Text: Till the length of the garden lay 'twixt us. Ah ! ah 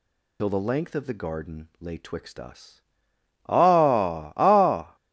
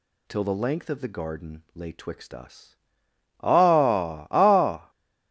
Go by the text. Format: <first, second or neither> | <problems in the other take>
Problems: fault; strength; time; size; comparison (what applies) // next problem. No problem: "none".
second | loses the start of "Till"; at 0.3 s; 65 ms